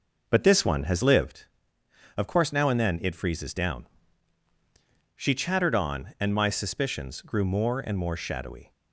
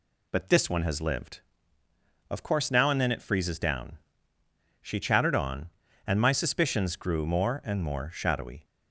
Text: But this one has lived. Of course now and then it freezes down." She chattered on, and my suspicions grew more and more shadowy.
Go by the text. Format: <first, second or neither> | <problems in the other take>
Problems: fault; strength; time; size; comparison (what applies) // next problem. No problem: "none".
second | starts louder than the rest; noticeable; until 1.3 s; 6 dB